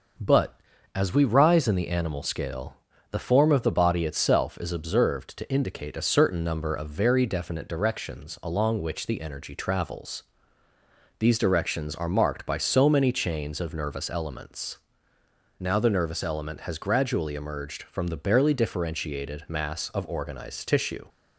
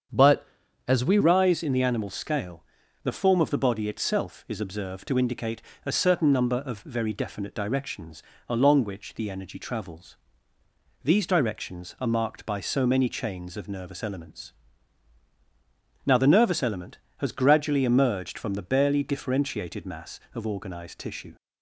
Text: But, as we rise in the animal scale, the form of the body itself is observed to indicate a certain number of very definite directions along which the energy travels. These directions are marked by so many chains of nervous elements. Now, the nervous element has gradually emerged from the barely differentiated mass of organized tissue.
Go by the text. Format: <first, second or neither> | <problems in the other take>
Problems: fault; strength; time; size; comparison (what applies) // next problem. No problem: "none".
first | starts louder than the rest; strong; until 1.5 s; 7.5 dB; noticeable in the first // changes voice at "rise"; from 1.2 s on; 20.1 s long // pauses between "indicate" and "a"; slight; at 5.6 s; 0.22 s long // pauses between "directions" and "along"; slight; at 8.2 s; 0.26 s long